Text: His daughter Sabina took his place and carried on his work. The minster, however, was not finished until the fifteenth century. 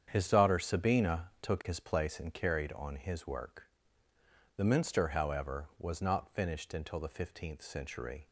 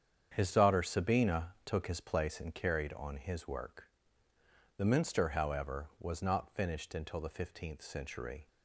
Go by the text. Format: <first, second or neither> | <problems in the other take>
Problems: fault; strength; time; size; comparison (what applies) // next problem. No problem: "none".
neither | starts louder than the rest; strong; the same in both